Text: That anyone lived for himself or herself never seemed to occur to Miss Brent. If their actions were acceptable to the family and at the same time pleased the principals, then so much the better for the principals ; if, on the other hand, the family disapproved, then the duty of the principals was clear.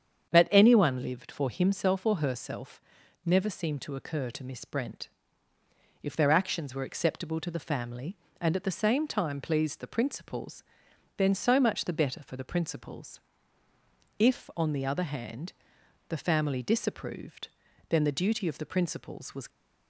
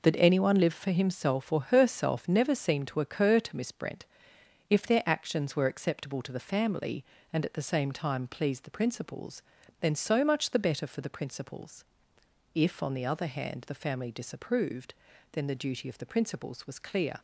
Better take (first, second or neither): second